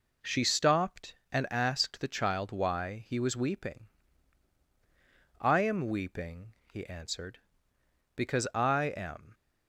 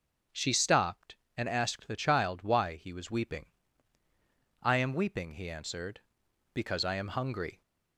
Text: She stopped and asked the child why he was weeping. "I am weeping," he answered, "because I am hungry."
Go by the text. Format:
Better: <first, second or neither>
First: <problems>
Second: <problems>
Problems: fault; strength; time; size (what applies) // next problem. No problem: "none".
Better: second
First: stops before "hungry"; at 9.3 s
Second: none